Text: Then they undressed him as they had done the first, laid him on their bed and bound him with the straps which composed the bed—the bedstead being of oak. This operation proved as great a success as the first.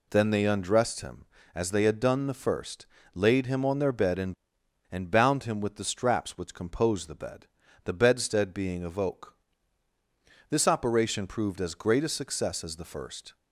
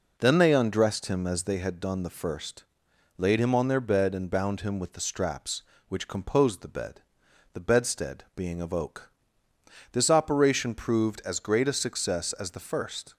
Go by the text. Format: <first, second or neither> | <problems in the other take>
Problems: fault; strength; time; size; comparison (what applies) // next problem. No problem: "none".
second | says "and" twice; at 4.9 s